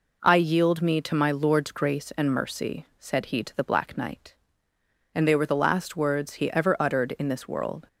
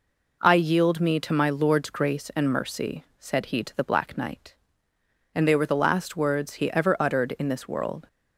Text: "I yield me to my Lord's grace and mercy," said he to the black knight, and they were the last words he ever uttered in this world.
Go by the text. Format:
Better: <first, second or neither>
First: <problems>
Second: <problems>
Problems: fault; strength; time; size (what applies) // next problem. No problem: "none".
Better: neither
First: none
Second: none